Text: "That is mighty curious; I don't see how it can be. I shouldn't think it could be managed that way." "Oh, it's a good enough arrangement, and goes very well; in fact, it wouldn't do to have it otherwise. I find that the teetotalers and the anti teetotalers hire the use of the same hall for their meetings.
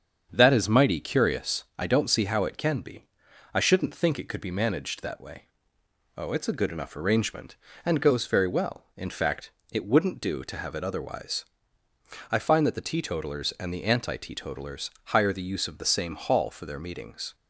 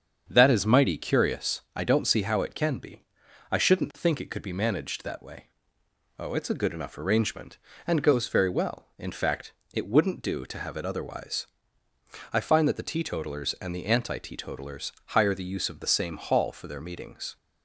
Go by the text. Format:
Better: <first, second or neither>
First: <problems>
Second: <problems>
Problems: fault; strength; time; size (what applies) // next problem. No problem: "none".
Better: neither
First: starts louder than the rest; strong; until 1.3 s; 7 dB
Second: starts louder than the rest; strong; until 1.3 s; 7 dB